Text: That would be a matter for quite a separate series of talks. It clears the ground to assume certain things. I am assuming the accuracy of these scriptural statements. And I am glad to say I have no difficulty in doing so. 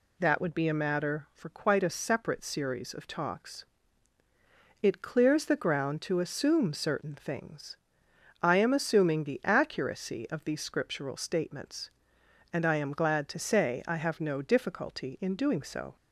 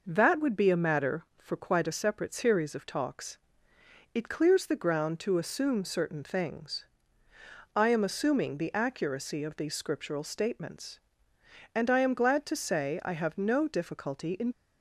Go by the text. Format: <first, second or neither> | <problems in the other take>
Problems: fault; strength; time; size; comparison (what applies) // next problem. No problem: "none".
first | stops before "doing so"; at 14.5 s